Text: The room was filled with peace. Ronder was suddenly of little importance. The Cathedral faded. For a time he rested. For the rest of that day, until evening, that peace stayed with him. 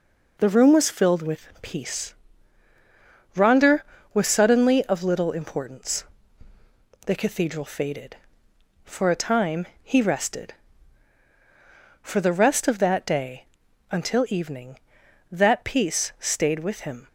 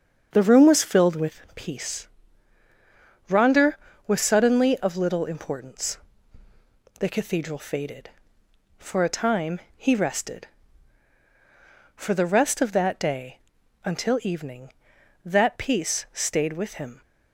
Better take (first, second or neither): first